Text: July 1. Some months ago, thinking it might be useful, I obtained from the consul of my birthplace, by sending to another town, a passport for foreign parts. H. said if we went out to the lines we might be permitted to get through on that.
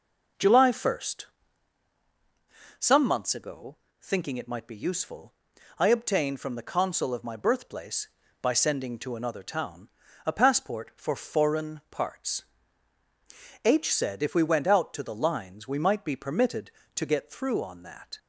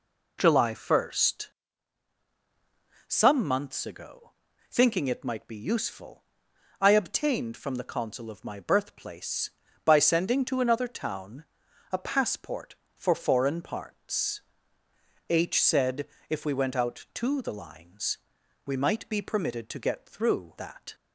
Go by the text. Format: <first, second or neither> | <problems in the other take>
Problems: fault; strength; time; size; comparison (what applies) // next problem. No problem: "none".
first | pauses between "said" and "if"; slight; at 16.0 s; 0.24 s long // pauses between "lines" and "we"; noticeable; at 18.1 s; 0.48 s long // skips "on"; at 20.5 s